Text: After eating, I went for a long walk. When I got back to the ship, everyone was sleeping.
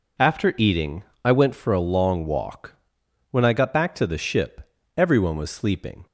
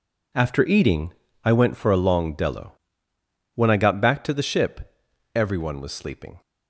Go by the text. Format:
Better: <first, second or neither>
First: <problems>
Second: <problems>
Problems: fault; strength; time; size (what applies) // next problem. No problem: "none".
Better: first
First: none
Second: says "dello" for "walk"; at 2.3 s